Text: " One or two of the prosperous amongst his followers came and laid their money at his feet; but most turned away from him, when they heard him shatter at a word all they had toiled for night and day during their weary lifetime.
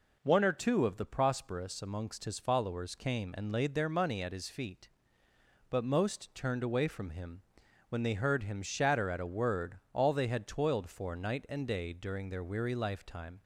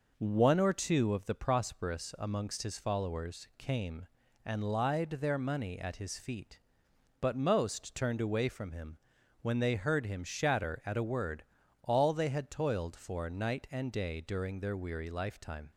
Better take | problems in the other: first | says "lied" for "laid"; at 4.6 s // pauses between "word" and "all"; at 11.4 s; 0.40 s long

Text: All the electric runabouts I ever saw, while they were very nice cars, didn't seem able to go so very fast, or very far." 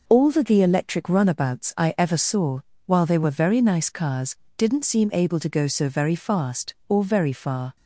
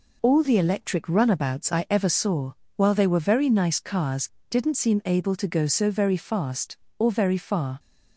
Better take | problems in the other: second | says "the" twice; at 0.4 s

